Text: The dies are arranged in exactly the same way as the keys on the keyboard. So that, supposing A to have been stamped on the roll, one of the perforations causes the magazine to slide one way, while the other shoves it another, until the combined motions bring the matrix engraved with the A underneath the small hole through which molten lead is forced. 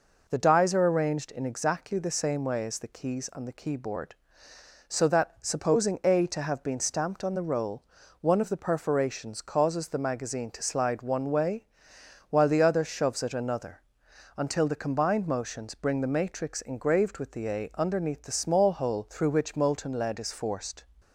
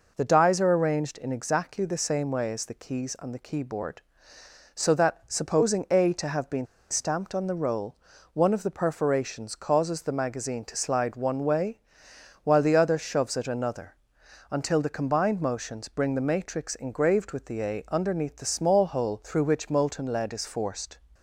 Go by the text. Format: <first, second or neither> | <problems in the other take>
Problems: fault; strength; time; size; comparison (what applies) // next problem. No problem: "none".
first | pauses between "been" and "stamped"; slight; at 6.6 s; 0.25 s long